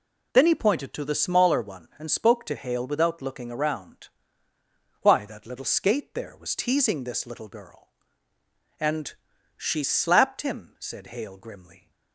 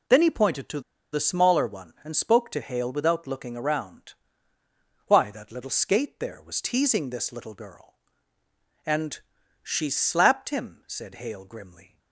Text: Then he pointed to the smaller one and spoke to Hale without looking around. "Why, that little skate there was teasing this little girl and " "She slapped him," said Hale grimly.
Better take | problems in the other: first | pauses between "to" and "the"; slight; at 0.8 s; 0.32 s long

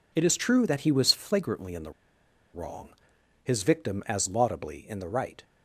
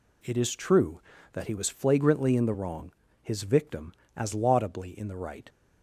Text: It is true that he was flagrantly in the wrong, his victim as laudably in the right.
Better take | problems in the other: second | pauses between "the" and "wrong"; noticeable; at 1.9 s; 0.63 s long

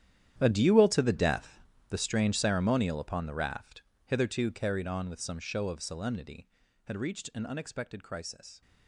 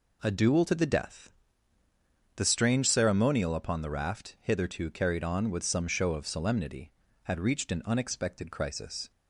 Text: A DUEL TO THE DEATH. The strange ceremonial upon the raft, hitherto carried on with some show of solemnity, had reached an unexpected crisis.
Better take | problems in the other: second | gets quieter; strong; throughout; 15.5 dB

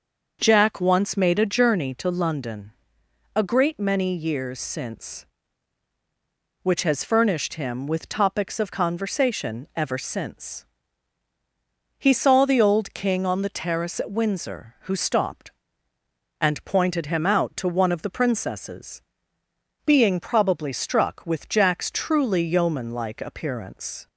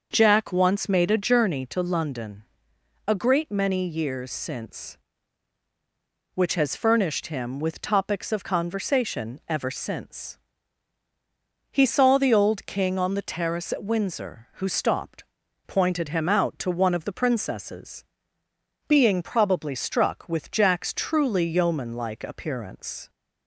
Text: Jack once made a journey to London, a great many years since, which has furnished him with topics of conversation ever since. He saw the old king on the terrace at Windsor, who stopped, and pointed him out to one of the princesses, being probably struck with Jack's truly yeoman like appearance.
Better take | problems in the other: first | starts louder than the rest; until 1.1 s; 6 dB; also in the first // skips "and"; at 15.4 s

